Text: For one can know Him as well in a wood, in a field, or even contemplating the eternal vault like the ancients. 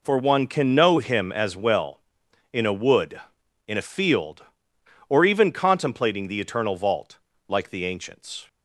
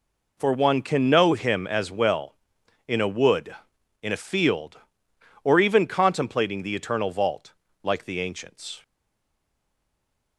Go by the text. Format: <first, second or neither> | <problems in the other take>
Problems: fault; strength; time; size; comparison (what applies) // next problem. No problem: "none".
first | pauses between "vault" and "like"; slight; at 7.5 s; 0.30 s long; slight in the first // stays silent after the last word; noticeable; from 8.8 s on; 1.5 s long